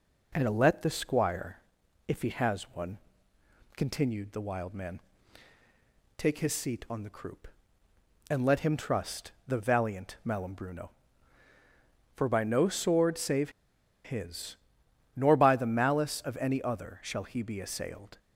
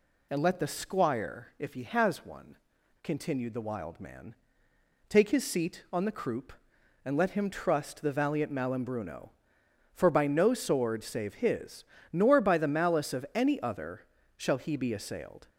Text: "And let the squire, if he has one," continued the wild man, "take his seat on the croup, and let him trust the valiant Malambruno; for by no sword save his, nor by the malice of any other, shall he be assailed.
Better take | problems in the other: second | pauses between "save" and "his"; noticeable; at 13.5 s; 0.53 s long

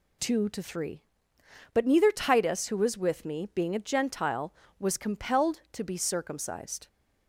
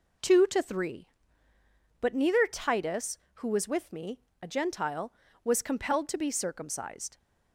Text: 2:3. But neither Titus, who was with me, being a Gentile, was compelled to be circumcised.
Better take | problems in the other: first | skips "being"; at 4.3 s

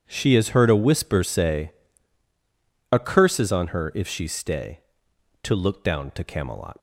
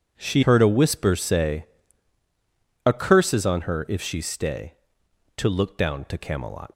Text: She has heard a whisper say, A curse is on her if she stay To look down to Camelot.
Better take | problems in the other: first | skips "has"; at 0.4 s

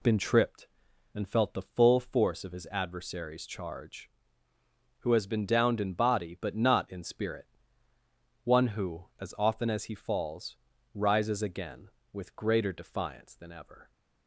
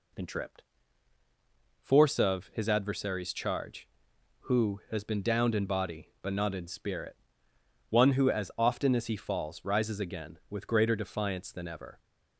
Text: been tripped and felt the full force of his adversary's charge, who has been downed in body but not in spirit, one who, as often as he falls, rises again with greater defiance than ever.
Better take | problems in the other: first | skips "and felt the full"; at 1.2 s

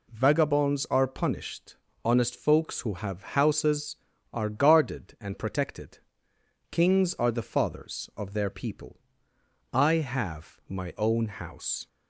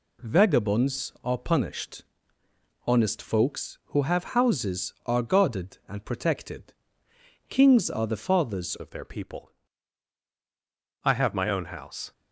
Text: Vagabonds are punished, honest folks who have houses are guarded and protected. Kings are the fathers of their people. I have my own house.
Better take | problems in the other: first | changes voice at "of"; from 8.7 s on; 3.4 s long

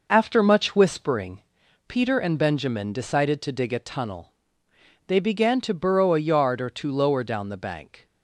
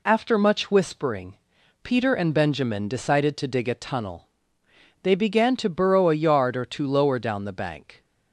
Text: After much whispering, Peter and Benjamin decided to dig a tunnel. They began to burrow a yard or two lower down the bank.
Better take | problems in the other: second | starts louder than the rest; noticeable; until 1.5 s; 5.5 dB

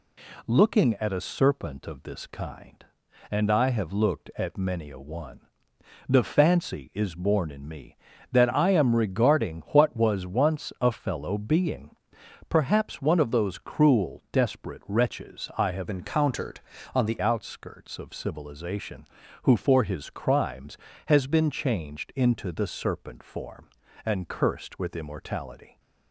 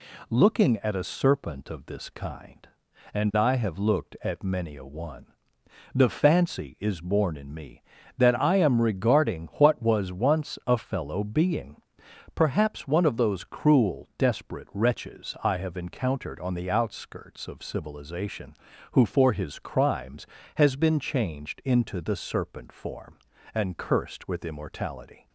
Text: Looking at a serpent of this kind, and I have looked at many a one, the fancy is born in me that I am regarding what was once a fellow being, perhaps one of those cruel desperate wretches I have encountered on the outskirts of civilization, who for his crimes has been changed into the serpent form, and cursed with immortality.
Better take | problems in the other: second | changes voice from "encountered" to "the"; from 15.9 to 17.1 s; 1.2 s long

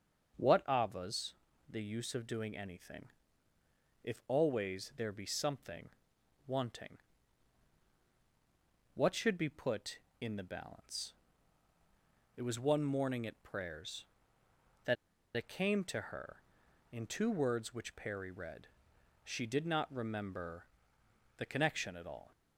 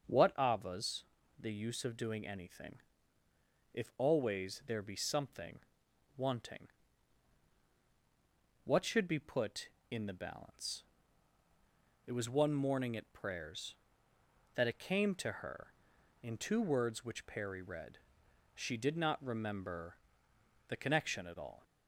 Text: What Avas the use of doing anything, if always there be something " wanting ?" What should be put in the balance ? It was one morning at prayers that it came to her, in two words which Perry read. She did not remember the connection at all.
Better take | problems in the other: second | starts louder than the rest; strong; until 1.7 s; 8 dB; strong in the second // pauses between "Avas" and "the"; slight; at 1.3 s; 0.36 s long; slight in the second // pauses between "that" and "it"; at 14.9 s; 0.41 s long // pauses between "remember" and "the"; noticeable; at 20.6 s; 0.72 s long; noticeable in the second

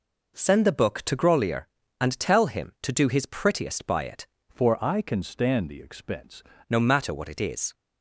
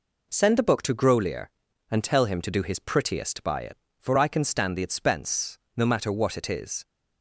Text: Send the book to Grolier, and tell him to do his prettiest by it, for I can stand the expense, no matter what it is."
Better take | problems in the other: second | changes voice from "for" to "expense"; from 4.4 to 6.4 s; 2.0 s long

